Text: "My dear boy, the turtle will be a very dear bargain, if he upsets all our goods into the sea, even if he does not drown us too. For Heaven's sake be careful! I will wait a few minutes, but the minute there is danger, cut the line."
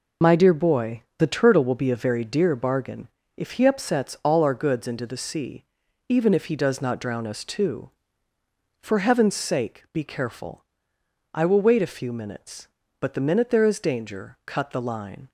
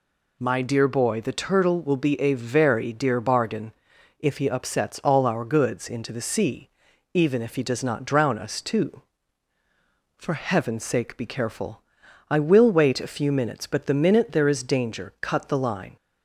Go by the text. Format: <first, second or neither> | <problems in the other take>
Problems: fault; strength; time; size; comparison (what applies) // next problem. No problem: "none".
second | loses the start of "My"; at 0.2 s; 30 ms